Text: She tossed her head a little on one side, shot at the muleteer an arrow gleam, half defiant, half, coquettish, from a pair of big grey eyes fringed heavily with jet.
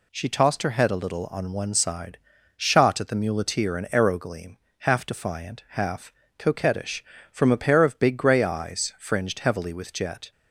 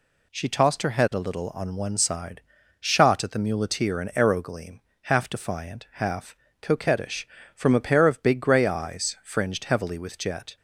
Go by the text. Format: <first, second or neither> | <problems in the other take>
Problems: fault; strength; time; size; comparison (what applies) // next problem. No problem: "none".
neither | none